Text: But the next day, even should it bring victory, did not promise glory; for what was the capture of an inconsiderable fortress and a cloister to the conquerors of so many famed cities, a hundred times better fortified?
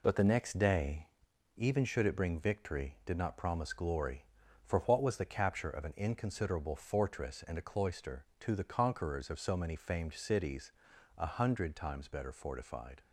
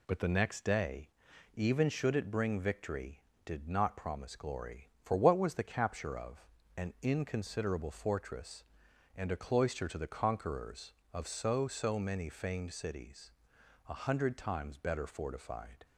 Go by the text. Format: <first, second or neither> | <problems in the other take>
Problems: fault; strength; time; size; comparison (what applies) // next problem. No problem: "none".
first | pauses between "of" and "an"; slight; at 6.4 s; 0.32 s long // says "so" twice; at 11.6 s